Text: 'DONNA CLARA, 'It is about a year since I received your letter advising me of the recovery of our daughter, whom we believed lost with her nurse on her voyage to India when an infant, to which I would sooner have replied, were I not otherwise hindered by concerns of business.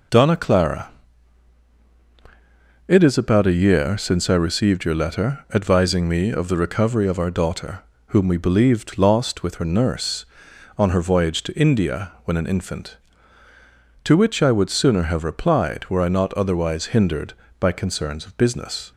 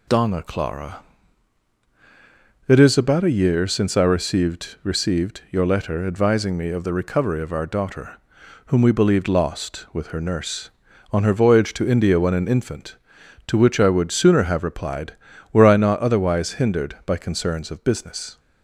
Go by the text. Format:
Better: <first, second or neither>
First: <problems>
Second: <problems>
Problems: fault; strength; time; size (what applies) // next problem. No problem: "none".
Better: first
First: none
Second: says "received" twice; at 4.8 s